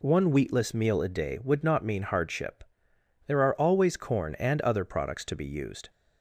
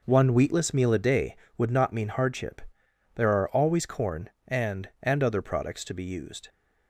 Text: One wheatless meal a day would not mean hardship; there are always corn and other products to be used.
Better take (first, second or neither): first